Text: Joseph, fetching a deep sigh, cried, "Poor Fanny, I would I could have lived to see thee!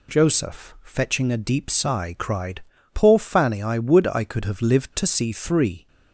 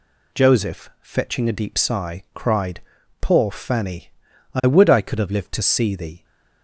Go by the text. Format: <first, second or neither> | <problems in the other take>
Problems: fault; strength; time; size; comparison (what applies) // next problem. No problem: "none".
second | says "three" for "thee"; at 5.3 s